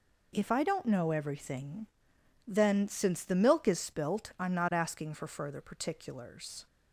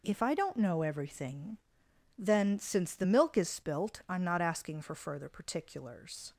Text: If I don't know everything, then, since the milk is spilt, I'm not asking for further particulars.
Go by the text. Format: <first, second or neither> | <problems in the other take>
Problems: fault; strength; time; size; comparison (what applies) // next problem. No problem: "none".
neither | none